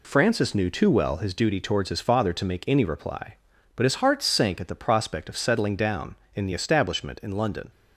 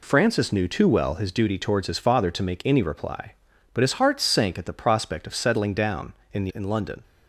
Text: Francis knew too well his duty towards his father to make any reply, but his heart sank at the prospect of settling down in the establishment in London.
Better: first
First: none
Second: skips "establishment"; at 6.5 s

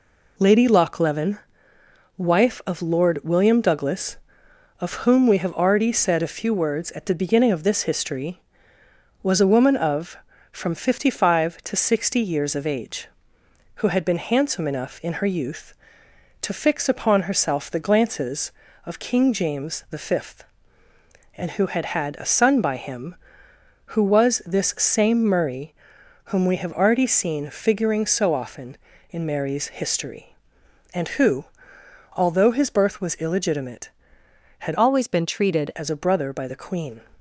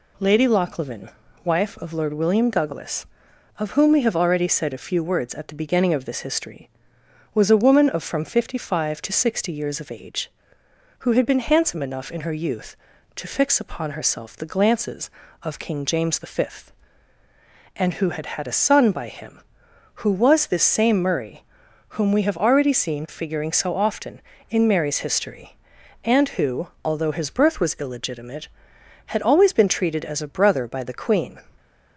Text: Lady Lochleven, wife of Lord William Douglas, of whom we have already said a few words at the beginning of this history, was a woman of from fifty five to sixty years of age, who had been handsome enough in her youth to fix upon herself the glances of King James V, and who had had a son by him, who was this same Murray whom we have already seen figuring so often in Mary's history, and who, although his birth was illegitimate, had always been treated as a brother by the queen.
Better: second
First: pauses between "Murray" and "whom"; noticeable; at 25.7 s; 0.52 s long // changes voice from "always" to "treated"; from 34.7 to 35.7 s; 1.0 s long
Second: pauses between "Murray" and "whom"; noticeable; at 21.4 s; 0.46 s long

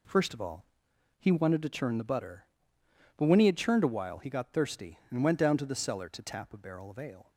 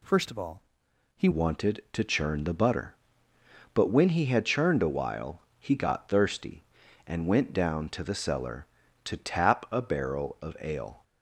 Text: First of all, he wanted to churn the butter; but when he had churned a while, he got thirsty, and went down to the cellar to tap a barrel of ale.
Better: first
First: none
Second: changes voice at "wanted"; from 1.3 s on; 9.7 s long

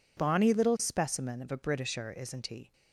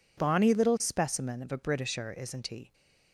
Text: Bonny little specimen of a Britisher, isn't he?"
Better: neither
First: none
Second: none

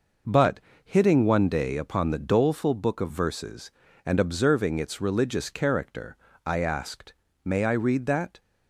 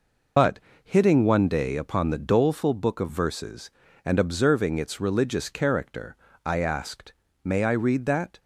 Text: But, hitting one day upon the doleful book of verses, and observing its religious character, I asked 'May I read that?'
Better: first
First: pauses between "asked" and "May"; slight; at 7.1 s; 0.30 s long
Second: loses the start of "But"; at 0.3 s; 120 ms // pauses between "asked" and "May"; slight; at 7.1 s; 0.30 s long

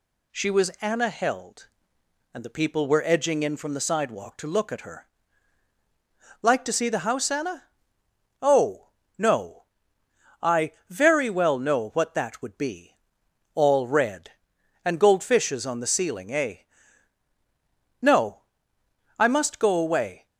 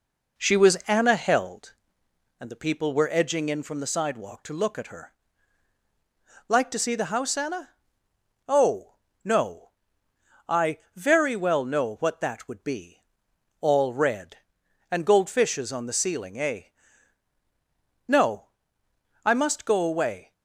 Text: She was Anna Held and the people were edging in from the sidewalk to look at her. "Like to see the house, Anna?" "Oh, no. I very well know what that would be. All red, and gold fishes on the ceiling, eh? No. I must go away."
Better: first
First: none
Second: starts louder than the rest; noticeable; until 1.7 s; 4 dB

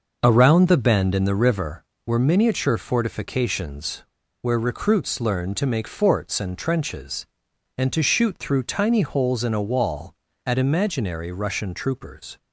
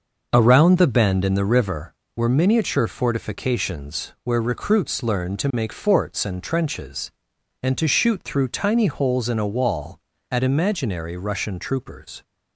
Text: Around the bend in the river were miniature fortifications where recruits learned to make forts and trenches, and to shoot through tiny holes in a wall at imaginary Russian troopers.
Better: second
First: starts louder than the rest; noticeable; until 1.2 s; 6 dB // pauses between "fortifications" and "where"; at 4.0 s; 0.39 s long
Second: starts louder than the rest; noticeable; until 1.3 s; 6 dB

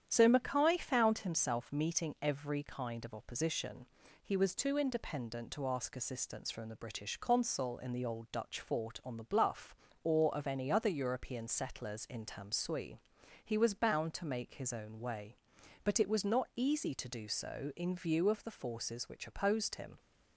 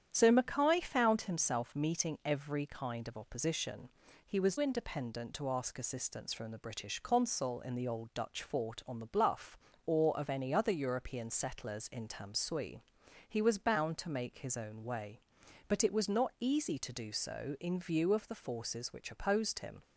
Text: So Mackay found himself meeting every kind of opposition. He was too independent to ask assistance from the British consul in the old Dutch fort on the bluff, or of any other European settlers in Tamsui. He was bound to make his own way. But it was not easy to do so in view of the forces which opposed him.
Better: first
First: starts louder than the rest; strong; until 1.0 s; 9 dB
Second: starts louder than the rest; strong; until 1.1 s; 9 dB // skips "too"; at 4.5 s

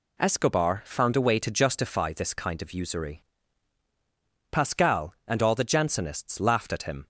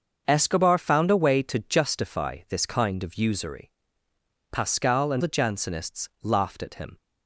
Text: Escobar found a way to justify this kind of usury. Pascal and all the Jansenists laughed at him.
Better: first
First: none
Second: starts louder than the rest; until 1.2 s; 6.5 dB // skips "all"; at 5.2 s

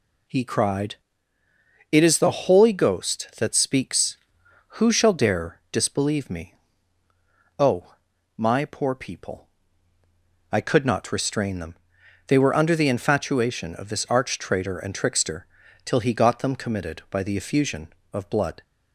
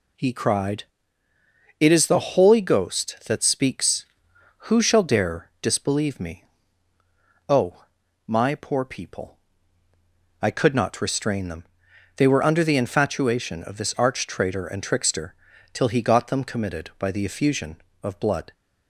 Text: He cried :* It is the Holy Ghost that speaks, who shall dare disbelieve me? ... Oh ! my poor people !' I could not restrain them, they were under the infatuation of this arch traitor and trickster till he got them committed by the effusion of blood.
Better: neither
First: pauses between "trickster" and "till"; at 15.4 s; 0.38 s long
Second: pauses between "trickster" and "till"; at 15.3 s; 0.38 s long

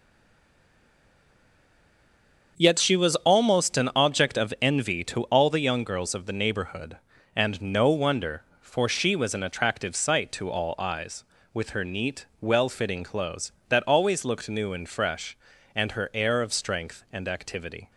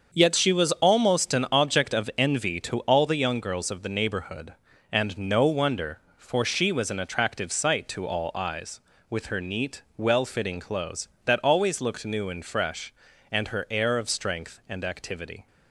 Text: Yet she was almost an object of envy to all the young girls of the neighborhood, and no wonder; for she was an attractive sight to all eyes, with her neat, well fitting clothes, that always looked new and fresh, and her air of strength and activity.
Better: second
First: stays silent before the first word; strong; until 2.5 s; 2.5 s long // starts louder than the rest; until 3.5 s; 6.5 dB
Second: starts louder than the rest; until 1.1 s; 6.5 dB

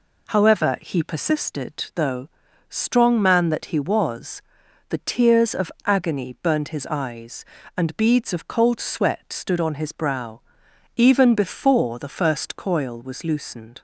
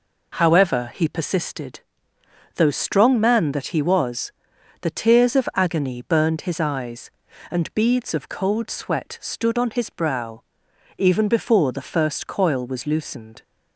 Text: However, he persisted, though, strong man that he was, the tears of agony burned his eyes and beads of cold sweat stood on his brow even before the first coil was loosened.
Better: neither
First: pauses between "brow" and "even"; noticeable; at 10.4 s; 0.56 s long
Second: pauses between "brow" and "even"; noticeable; at 10.4 s; 0.56 s long

